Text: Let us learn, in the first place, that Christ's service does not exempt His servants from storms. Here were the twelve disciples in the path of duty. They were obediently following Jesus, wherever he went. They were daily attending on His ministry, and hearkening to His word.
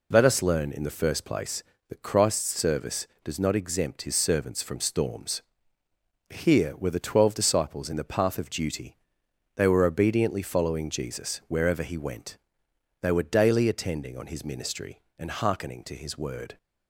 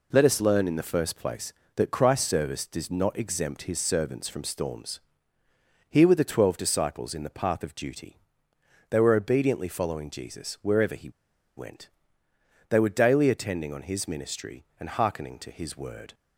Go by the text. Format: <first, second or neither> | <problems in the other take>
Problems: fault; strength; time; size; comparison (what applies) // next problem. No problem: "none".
first | pauses between "he" and "went"; noticeable; at 11.0 s; 0.47 s long